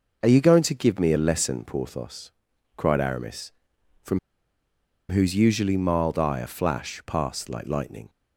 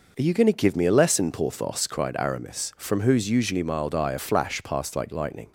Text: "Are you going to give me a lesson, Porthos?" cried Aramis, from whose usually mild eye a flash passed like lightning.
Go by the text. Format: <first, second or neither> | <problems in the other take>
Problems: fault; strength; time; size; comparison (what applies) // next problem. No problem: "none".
second | pauses between "from" and "whose"; noticeable; at 4.1 s; 0.92 s long